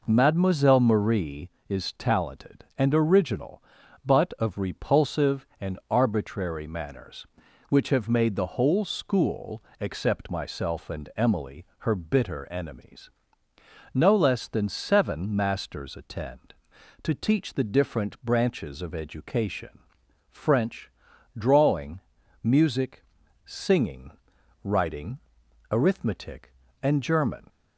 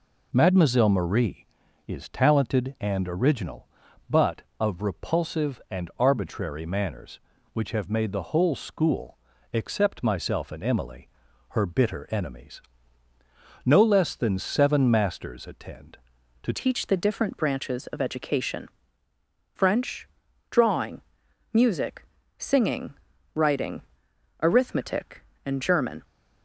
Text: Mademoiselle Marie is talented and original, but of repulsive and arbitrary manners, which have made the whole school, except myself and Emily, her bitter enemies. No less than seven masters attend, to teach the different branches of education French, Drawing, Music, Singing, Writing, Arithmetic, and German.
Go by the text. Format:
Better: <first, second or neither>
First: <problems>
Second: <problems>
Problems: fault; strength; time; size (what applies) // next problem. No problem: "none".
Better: first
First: pauses between "education" and "French"; noticeable; at 19.7 s; 0.50 s long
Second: changes voice at "teach"; from 16.5 s on; 9.5 s long // pauses between "education" and "French"; noticeable; at 18.6 s; 0.84 s long